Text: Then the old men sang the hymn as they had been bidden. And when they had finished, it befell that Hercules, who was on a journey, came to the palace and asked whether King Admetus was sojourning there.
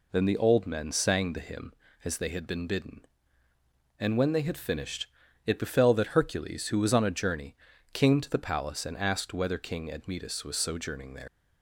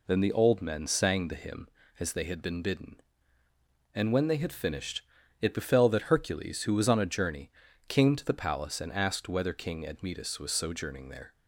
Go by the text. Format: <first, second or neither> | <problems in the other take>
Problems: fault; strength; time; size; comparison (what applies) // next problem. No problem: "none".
second | leaves "there" unfinished; at 11.2 s; 95 ms